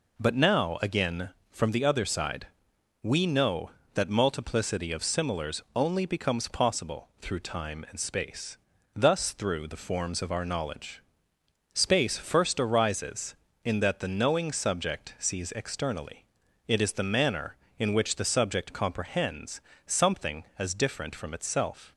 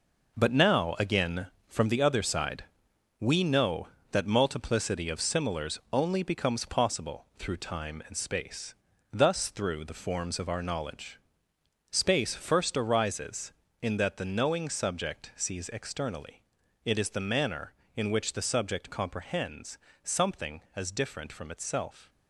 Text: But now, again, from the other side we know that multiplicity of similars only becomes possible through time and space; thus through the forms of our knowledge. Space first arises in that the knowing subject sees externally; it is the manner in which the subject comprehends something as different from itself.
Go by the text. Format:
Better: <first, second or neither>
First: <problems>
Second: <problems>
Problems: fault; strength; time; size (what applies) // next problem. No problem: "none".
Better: first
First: pauses between "side" and "we"; noticeable; at 2.4 s; 0.56 s long // pauses between "similars" and "only"; slight; at 5.6 s; 0.16 s long // pauses between "comprehends" and "something"; slight; at 19.6 s; 0.24 s long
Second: gets quieter; strong; throughout; 8.5 dB // pauses between "side" and "we"; noticeable; at 2.6 s; 0.56 s long // pauses between "similars" and "only"; slight; at 5.7 s; 0.16 s long // pauses between "comprehends" and "something"; slight; at 19.7 s; 0.24 s long